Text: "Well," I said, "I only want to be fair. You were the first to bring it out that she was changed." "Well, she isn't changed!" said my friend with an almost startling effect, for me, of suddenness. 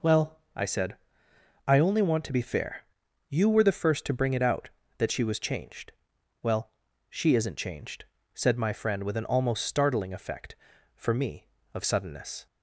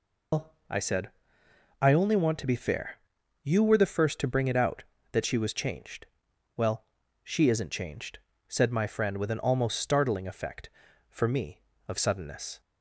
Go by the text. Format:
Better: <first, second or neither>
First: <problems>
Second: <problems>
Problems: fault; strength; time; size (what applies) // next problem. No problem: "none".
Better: first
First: none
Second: loses the start of "Well"; at 0.3 s; 165 ms